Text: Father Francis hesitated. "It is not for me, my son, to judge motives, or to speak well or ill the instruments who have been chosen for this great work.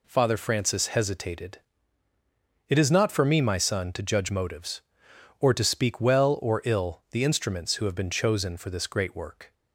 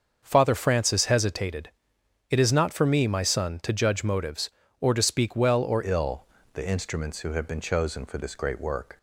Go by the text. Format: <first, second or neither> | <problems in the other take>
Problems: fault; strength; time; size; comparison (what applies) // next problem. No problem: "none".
first | starts louder than the rest; until 1.2 s; 6.5 dB // changes voice at "ill"; from 5.8 s on; 3.1 s long // pauses between "ill" and "the"; slight; at 6.2 s; 0.30 s long